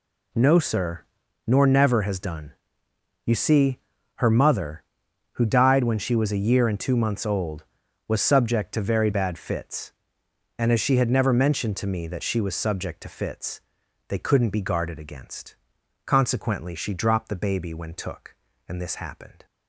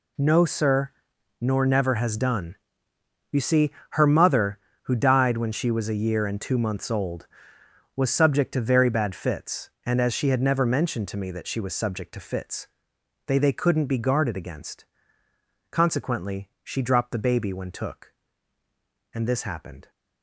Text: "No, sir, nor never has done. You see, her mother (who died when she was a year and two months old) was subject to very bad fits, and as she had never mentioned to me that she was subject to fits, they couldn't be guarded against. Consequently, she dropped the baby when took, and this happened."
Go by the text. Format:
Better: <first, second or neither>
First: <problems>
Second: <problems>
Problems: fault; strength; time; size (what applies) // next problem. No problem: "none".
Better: first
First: none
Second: says "they" twice; at 13.3 s